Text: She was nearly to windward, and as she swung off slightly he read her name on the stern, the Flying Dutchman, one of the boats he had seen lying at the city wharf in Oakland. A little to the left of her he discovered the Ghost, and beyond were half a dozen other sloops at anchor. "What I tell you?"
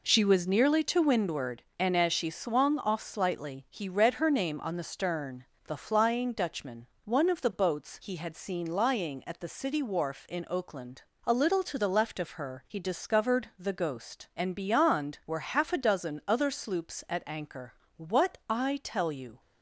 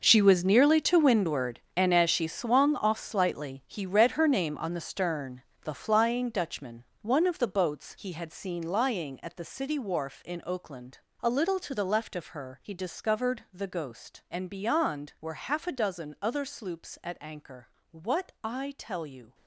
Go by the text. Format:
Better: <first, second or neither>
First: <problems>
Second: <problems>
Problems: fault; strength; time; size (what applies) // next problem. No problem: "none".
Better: first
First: none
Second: gets quieter; strong; throughout; 13.5 dB